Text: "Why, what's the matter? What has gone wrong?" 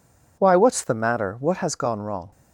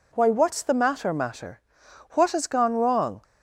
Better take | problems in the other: first | says "matter" twice; at 1.1 s

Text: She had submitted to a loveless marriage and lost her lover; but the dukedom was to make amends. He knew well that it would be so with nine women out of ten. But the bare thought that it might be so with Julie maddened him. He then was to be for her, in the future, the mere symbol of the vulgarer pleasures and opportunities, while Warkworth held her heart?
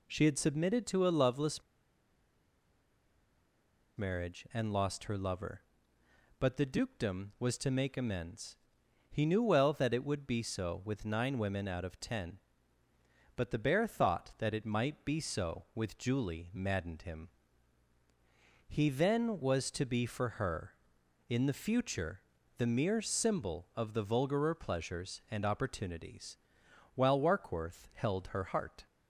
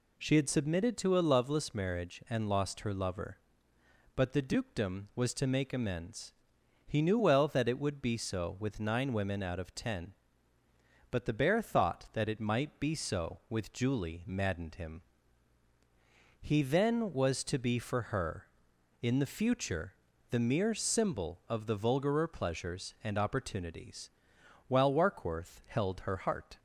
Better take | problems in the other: second | pauses between "loveless" and "marriage"; strong; at 1.6 s; 2.3 s long

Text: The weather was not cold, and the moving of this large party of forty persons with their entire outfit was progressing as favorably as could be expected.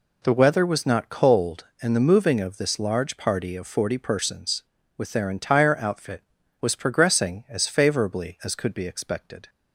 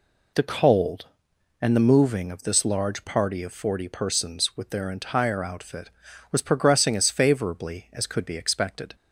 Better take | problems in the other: first | skips "weather was not"; at 0.4 s

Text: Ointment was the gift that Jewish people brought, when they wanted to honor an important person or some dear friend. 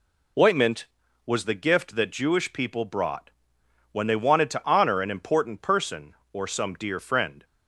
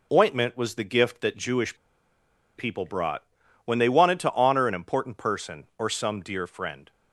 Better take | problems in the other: first | pauses between "Jewish" and "people"; noticeable; at 1.7 s; 0.81 s long

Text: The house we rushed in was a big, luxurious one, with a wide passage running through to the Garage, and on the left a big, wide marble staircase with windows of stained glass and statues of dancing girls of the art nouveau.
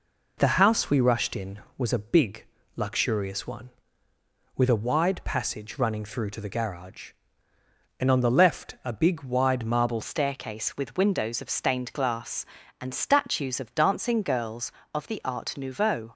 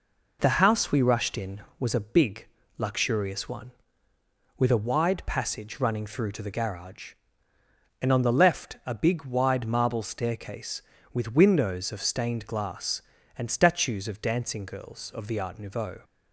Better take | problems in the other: second | changes voice at "staircase"; from 10.0 s on; 6.1 s long

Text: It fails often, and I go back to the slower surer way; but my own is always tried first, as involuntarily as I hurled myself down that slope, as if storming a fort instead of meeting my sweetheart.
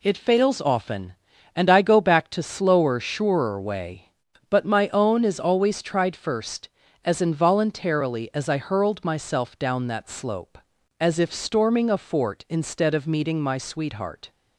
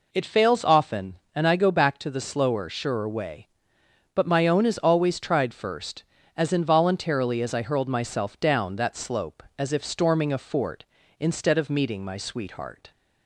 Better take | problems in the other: second | skips "the"; at 2.4 s

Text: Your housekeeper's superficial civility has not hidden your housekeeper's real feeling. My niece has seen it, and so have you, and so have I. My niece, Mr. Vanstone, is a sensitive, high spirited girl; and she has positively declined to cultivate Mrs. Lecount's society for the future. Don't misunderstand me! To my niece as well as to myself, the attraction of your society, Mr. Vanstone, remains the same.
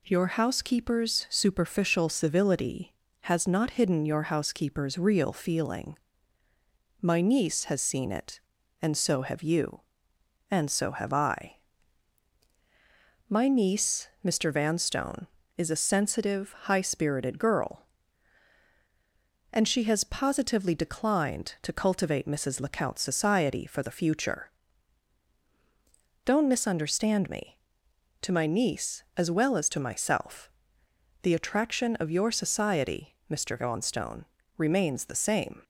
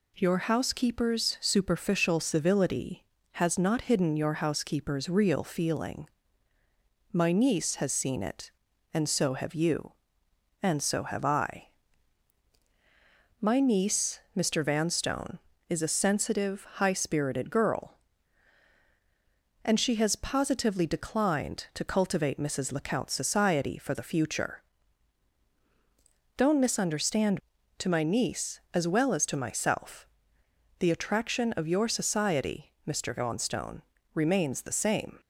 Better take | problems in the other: first | skips "me"; at 27.5 s

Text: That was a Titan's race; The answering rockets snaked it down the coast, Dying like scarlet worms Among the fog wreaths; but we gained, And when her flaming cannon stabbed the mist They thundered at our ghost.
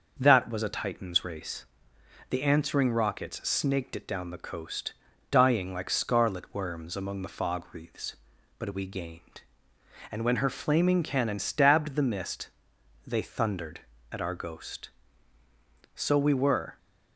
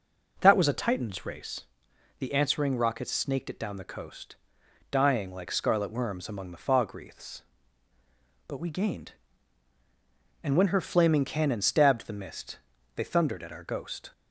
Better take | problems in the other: second | starts louder than the rest; until 1.2 s; 6.5 dB // pauses between "mist" and "They"; noticeable; at 12.4 s; 0.58 s long; slight in the second // goes on to say "So we were"; noticeable; from 15.9 s on; 0.84 s long

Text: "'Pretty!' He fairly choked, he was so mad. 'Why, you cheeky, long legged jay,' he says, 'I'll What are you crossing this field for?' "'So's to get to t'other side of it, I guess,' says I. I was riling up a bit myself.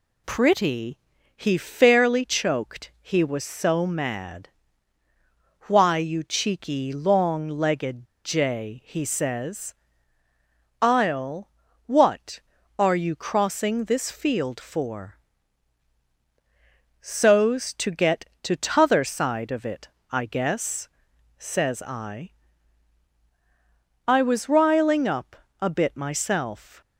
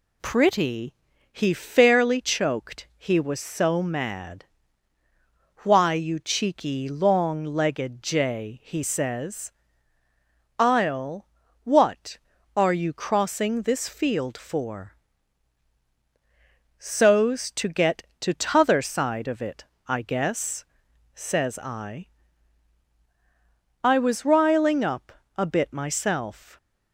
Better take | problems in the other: second | pauses between "legged" and "jay"; slight; at 8.0 s; 0.18 s long // pauses between "I'll" and "What"; slight; at 11.5 s; 0.34 s long; slight in the second // pauses between "up" and "a"; slight; at 25.3 s; 0.24 s long; slight in the second

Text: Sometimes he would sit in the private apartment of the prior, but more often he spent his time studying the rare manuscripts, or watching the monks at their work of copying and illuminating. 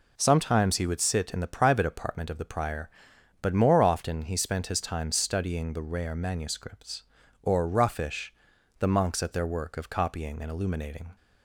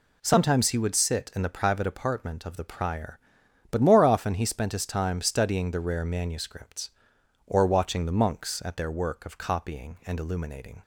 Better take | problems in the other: second | says "roughish" for "watching"; at 7.6 s

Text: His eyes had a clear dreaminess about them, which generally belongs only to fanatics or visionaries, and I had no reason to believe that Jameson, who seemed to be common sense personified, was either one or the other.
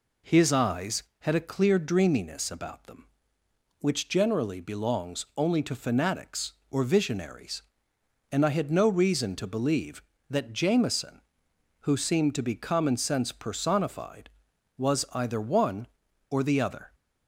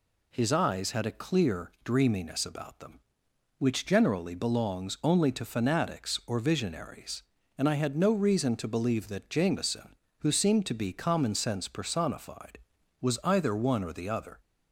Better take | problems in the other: neither | none

